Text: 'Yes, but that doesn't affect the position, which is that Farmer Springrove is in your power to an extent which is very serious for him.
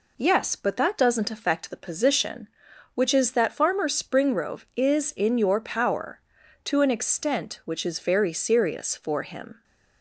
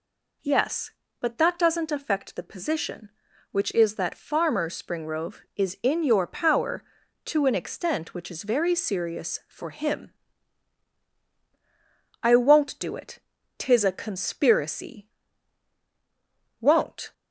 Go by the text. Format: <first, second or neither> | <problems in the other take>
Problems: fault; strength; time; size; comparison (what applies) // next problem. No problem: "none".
first | goes on to say "I won't do it tis a conspiracy Won't"; strong; from 12.2 s on; 4.9 s long